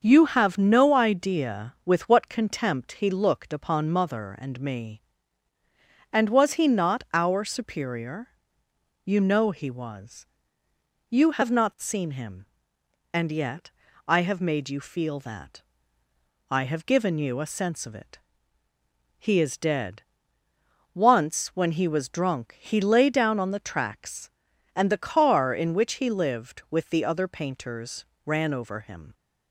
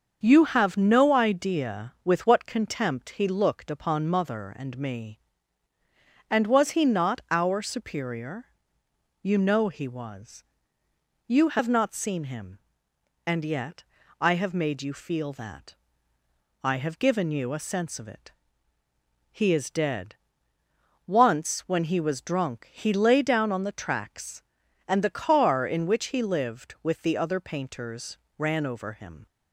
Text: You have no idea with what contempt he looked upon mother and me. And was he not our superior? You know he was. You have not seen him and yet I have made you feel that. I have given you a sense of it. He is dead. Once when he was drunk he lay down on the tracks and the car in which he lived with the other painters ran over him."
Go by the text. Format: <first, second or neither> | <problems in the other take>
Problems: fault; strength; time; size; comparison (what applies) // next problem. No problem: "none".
neither | starts louder than the rest; the same in both // pauses between "yet" and "I"; slight; the same in both // pauses between "painters" and "ran"; slight; the same in both